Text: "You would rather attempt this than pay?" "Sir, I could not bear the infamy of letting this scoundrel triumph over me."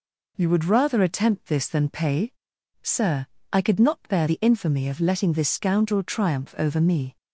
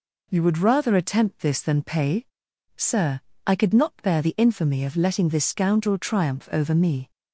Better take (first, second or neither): neither